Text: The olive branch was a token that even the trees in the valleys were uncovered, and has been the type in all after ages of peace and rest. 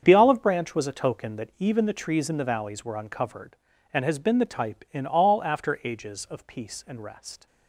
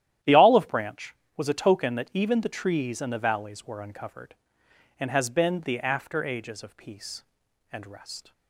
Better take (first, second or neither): first